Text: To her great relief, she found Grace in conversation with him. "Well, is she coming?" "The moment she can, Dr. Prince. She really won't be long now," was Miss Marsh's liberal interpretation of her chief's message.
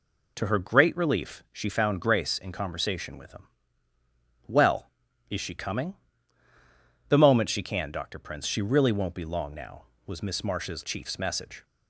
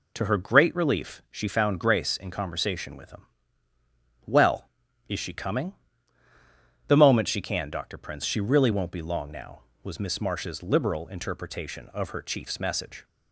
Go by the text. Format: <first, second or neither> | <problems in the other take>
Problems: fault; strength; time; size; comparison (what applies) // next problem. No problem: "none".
second | skips "liberal interpretation of her"; at 10.8 s